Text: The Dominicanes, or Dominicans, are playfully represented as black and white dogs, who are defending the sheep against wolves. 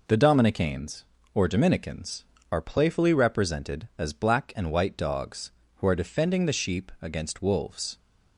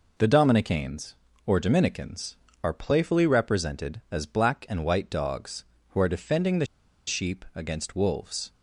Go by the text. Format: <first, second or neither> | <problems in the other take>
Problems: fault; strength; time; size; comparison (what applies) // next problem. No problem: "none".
first | pauses between "the" and "sheep"; at 6.6 s; 0.42 s long